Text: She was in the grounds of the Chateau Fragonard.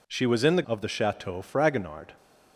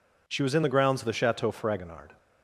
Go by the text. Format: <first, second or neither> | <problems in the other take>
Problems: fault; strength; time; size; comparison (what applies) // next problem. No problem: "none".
second | skips "grounds"; at 0.6 s